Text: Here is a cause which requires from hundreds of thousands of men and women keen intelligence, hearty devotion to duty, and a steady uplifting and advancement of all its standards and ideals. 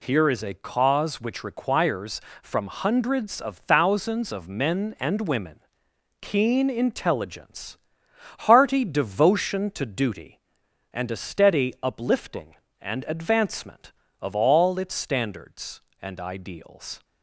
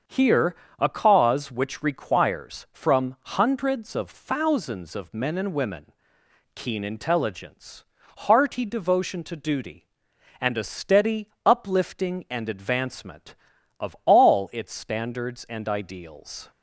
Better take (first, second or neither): first